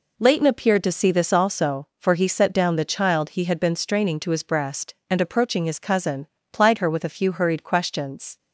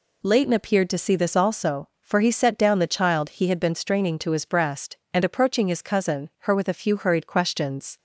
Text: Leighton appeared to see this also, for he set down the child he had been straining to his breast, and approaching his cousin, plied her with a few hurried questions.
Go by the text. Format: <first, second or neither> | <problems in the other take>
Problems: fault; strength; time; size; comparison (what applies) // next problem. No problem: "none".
first | skips "plied"; at 6.3 s